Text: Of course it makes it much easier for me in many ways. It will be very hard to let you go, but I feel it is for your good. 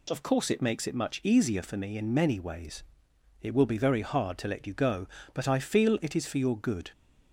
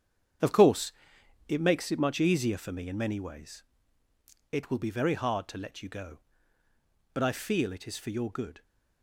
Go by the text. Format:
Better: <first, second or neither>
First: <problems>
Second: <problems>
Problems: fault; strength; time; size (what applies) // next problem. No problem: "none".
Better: first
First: none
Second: gets quieter; strong; throughout; 10.5 dB // pauses between "course" and "it"; noticeable; at 0.9 s; 0.56 s long